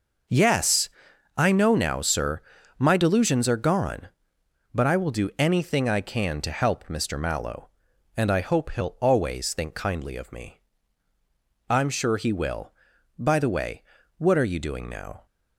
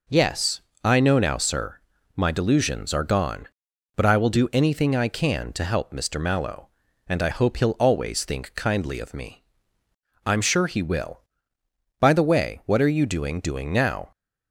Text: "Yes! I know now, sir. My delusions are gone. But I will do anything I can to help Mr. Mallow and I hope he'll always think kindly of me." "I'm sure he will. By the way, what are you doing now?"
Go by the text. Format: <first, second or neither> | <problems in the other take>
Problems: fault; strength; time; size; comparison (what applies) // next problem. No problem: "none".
first | says "doing" twice; at 13.3 s